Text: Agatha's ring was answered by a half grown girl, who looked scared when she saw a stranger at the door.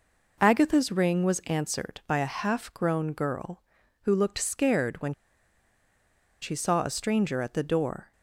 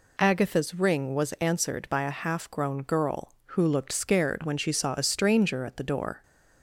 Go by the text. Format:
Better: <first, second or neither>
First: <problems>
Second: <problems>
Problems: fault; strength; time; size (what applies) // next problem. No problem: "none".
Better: second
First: pauses between "when" and "she"; strong; at 5.1 s; 1.2 s long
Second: none